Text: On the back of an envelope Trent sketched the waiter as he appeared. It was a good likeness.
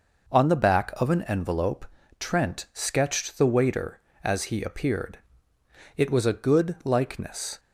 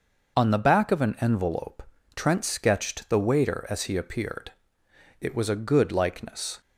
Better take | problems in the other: neither | pauses between "envelope" and "Trent"; slight; the same in both

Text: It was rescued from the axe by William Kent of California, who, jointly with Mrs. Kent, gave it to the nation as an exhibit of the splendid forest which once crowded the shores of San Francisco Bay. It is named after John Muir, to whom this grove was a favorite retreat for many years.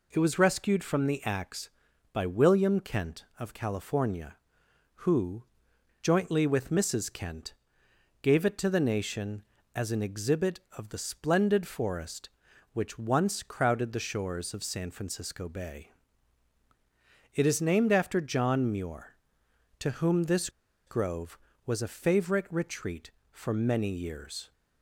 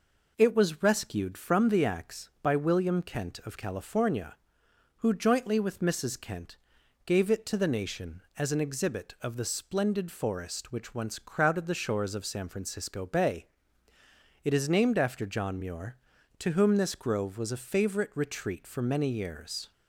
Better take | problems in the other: second | pauses between "this" and "grove"; at 20.4 s; 0.38 s long

